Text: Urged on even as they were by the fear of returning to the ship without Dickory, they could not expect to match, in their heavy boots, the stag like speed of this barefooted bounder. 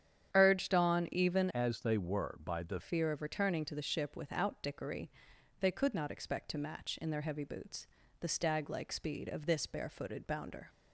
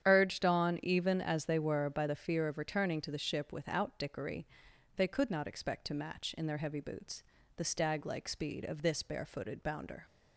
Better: second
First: starts louder than the rest; strong; until 1.3 s; 9 dB // changes voice from "as" to "the"; from 1.5 to 2.7 s; 1.2 s long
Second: starts louder than the rest; strong; until 1.0 s; 9 dB

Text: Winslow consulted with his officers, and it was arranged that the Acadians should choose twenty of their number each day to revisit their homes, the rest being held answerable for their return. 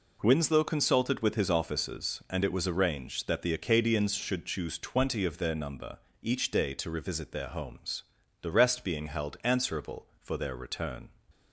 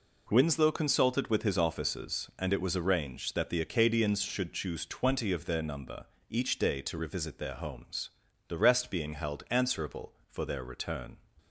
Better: neither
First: pauses between "number" and "each"; slight; at 5.9 s; 0.22 s long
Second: pauses between "number" and "each"; slight; at 6.0 s; 0.22 s long

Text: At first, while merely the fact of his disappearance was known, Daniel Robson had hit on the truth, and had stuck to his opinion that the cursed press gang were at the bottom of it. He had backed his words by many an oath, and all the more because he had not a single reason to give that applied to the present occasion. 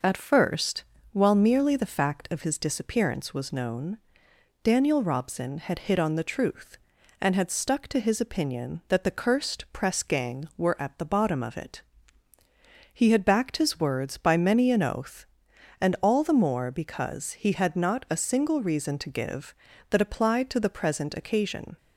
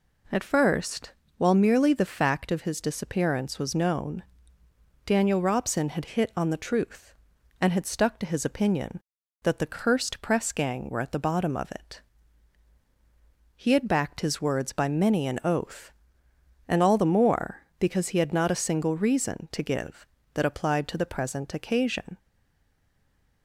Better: first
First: none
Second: stays silent after the last word; noticeable; from 22.1 s on; 1.3 s long

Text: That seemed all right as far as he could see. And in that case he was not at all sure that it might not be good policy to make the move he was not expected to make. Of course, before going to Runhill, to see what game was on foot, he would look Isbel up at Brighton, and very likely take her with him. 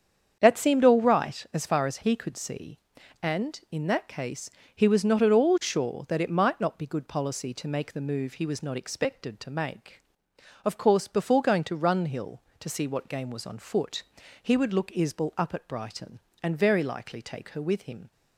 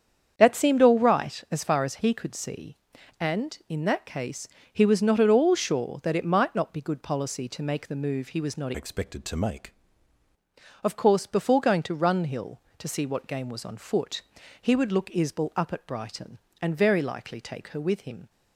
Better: first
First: starts louder than the rest; strong; until 1.4 s; 7.5 dB // pauses between "case" and "he"; slight; at 4.5 s; 0.24 s long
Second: starts louder than the rest; strong; until 1.3 s; 8 dB // pauses between "case" and "he"; slight; at 4.4 s; 0.24 s long // changes voice from "expected" to "make"; from 8.7 to 9.7 s; 1.0 s long

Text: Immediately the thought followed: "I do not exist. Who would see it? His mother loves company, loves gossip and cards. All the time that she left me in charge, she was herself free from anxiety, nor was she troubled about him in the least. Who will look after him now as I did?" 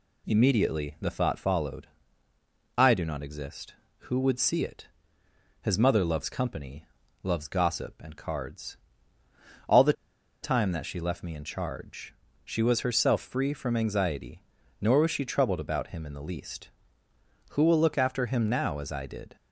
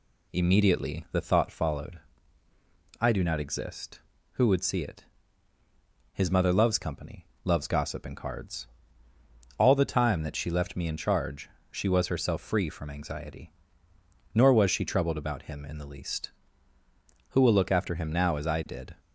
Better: second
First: pauses between "the" and "time"; noticeable; at 9.9 s; 0.50 s long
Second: none

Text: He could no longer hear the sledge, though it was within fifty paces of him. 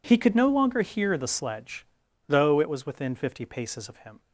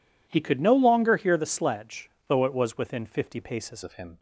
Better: first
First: none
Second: changes voice at "of"; from 3.8 s on; 0.3 s long

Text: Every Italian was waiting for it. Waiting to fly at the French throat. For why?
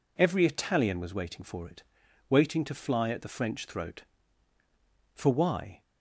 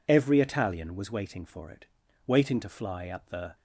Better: first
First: none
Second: stops before "French throat For why"; at 3.5 s

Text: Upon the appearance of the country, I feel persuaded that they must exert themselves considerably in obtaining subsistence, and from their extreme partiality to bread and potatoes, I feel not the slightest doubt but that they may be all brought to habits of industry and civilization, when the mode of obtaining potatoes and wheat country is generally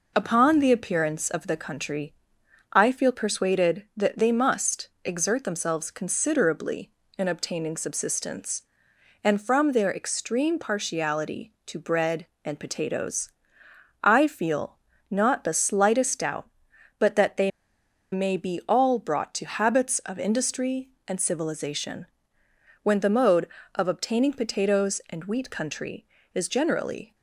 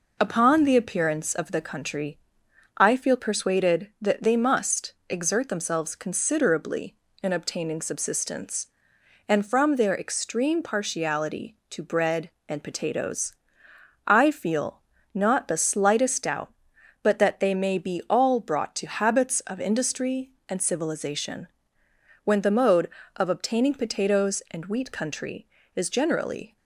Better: second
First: pauses between "feel" and "not"; slight; at 14.7 s; 0.34 s long // pauses between "they" and "may"; noticeable; at 17.5 s; 0.62 s long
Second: pauses between "feel" and "not"; slight; at 14.7 s; 0.34 s long

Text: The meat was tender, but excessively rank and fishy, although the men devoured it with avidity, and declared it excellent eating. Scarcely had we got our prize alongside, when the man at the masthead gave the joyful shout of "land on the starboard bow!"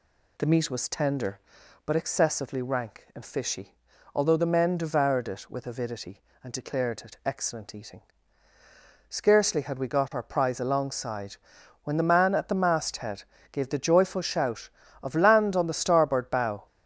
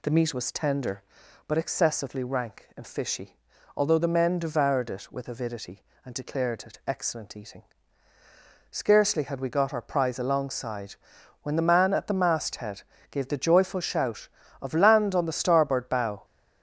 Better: neither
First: pauses between "masthead" and "gave"; slight; at 13.2 s; 0.26 s long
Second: pauses between "masthead" and "gave"; slight; at 12.8 s; 0.26 s long

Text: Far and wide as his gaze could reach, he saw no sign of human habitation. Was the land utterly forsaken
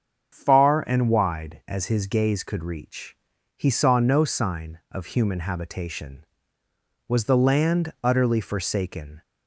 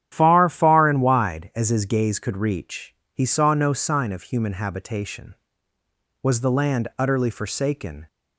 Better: first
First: starts louder than the rest; strong; until 1.3 s; 7 dB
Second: starts louder than the rest; strong; until 1.1 s; 10.5 dB // says "Far" twice; at 0.4 s

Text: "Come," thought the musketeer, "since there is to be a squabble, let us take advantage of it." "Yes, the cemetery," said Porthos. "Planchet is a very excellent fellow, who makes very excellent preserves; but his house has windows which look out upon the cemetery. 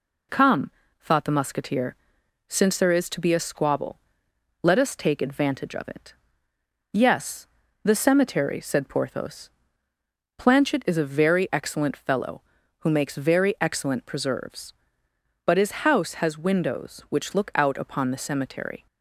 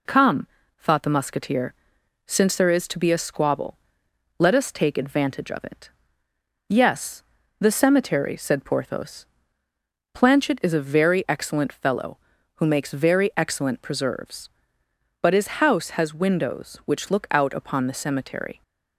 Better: neither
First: none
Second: none

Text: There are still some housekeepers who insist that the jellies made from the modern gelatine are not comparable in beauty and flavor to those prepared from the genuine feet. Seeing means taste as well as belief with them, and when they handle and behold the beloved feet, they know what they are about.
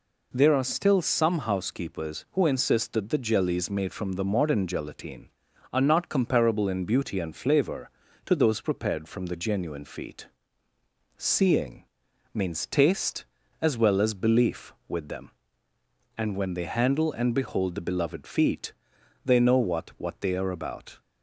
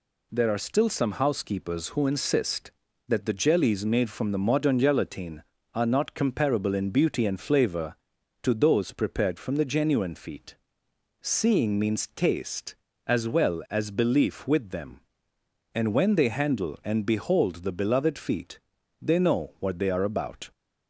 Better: second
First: pauses between "Seeing" and "means"; noticeable; at 11.8 s; 0.50 s long // says "what" twice; at 19.9 s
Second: none

